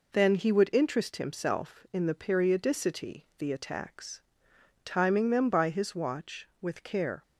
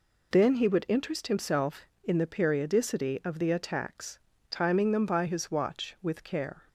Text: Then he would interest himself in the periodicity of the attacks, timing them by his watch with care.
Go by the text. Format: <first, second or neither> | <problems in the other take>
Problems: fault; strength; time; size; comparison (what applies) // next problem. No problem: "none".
second | skips "of"; at 3.3 s